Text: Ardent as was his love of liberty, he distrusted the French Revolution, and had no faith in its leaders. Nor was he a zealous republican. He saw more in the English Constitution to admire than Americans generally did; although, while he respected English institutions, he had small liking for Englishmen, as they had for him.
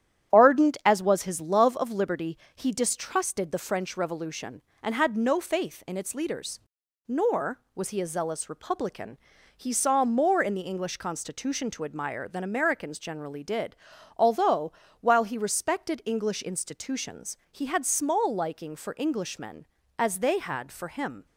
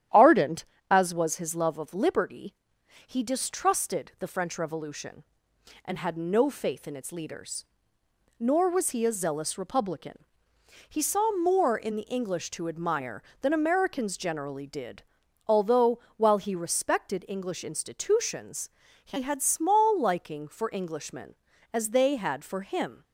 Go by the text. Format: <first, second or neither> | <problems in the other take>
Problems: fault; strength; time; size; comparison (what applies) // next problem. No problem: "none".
first | starts louder than the rest; strong; until 1.3 s; 11 dB; strong in the first // skips "Constitution"; at 12.5 s